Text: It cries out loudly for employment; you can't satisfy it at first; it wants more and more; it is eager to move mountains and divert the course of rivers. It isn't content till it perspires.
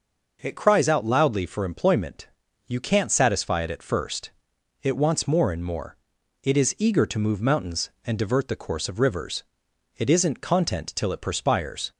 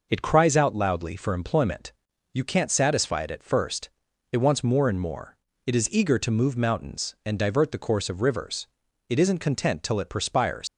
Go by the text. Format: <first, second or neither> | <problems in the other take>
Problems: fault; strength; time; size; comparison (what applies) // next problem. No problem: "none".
first | leaves "perspires" unfinished; at 10.6 s; 110 ms